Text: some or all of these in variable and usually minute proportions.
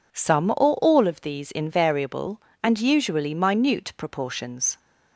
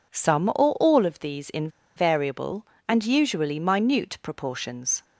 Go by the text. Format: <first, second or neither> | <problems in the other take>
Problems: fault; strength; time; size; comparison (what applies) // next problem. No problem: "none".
first | pauses between "in" and "variable"; slight; at 1.6 s; 0.27 s long